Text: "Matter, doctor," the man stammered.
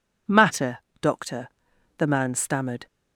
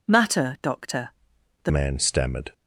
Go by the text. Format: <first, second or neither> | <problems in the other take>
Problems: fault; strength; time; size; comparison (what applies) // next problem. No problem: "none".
first | changes voice at "man"; from 1.6 s on; 0.9 s long